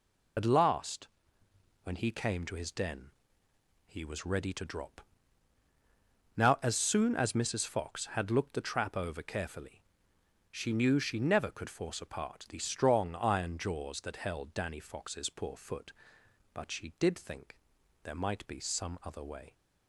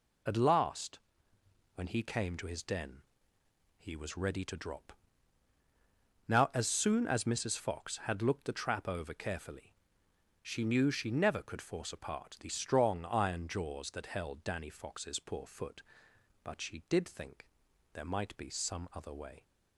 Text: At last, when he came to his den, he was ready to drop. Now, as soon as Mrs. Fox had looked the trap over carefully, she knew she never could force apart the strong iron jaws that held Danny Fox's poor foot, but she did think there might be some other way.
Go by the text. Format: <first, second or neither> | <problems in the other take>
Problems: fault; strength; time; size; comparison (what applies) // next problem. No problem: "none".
second | loses the start of "At"; at 0.3 s; 35 ms // pauses between "think" and "there"; noticeable; at 17.5 s; 0.48 s long; noticeable in the second